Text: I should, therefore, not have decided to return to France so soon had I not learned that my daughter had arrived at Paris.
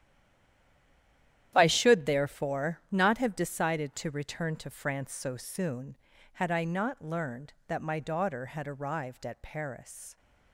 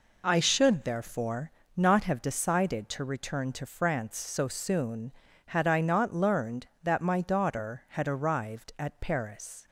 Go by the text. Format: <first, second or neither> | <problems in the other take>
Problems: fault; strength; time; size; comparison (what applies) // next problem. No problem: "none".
second | stays silent before the first word; noticeable; until 1.5 s; 1.5 s long // starts louder than the rest; strong; until 2.5 s; 11 dB